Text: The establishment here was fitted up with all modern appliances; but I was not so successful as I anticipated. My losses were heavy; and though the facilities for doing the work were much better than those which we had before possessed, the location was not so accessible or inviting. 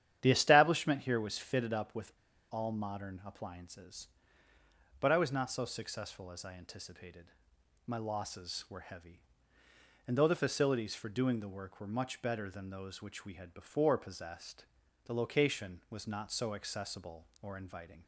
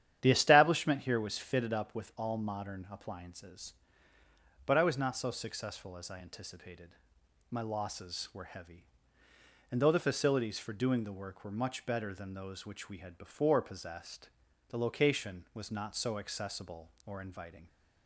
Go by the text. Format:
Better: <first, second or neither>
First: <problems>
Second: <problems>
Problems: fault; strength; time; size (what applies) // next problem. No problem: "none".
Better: second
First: starts louder than the rest; strong; until 1.2 s; 10 dB // pauses between "with" and "all"; at 2.1 s; 0.40 s long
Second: starts louder than the rest; strong; until 1.2 s; 10 dB